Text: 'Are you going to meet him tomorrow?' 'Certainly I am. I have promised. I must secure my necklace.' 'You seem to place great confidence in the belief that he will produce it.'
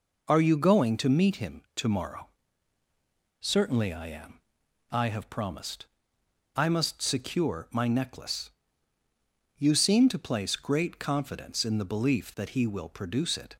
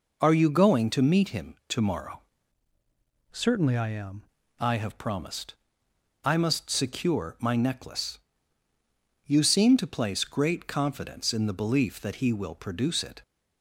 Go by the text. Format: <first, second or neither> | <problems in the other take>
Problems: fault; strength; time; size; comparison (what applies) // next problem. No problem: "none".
first | changes voice from "Certainly" to "am"; from 3.3 to 4.2 s; 0.9 s long